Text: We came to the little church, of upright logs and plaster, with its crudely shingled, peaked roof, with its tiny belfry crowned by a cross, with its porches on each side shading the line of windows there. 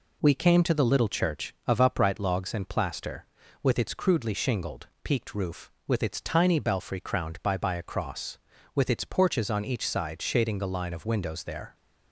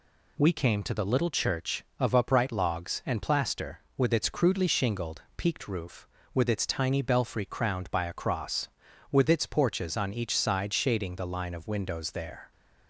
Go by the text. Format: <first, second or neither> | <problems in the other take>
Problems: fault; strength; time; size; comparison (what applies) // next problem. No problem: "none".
second | says "by" twice; at 7.5 s